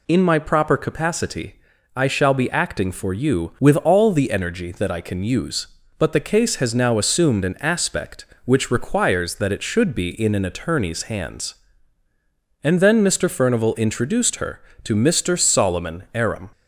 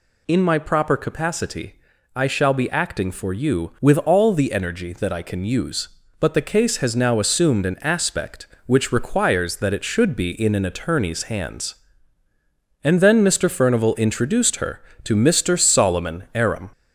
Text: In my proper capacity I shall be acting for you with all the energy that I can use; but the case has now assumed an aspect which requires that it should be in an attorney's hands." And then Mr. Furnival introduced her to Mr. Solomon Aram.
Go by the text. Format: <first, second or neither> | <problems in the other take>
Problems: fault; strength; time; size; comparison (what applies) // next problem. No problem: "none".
first | gets louder; throughout; 3.5 dB // pauses between "capacity" and "I"; at 1.7 s; 0.40 s long; also in the first